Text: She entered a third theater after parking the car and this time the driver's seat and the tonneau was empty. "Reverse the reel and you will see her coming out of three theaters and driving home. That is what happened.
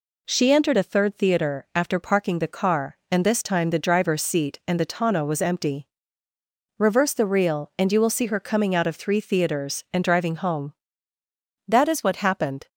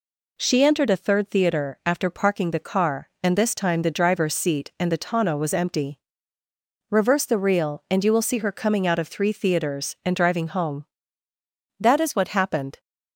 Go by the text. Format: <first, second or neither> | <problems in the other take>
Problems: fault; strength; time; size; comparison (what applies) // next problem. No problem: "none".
neither | none